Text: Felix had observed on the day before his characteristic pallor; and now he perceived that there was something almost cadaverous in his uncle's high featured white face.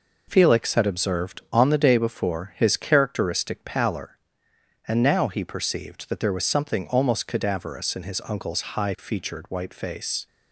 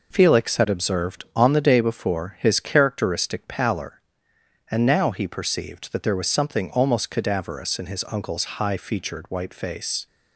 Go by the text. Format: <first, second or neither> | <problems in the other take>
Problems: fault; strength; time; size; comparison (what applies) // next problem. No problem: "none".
neither | none